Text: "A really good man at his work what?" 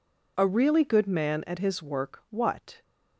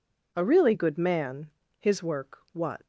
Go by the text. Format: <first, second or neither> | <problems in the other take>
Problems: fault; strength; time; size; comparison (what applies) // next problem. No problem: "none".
first | skips "at"; at 1.6 s // pauses between "work" and "what"; slight; at 2.3 s; 0.15 s long